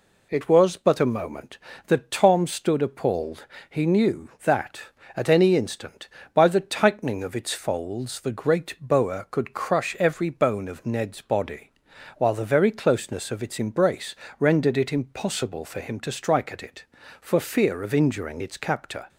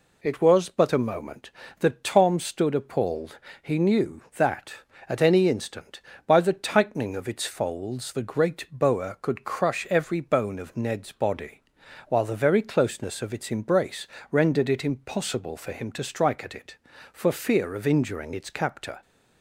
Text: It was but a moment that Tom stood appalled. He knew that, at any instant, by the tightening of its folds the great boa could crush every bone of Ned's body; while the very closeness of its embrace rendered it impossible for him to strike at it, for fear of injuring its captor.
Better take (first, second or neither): neither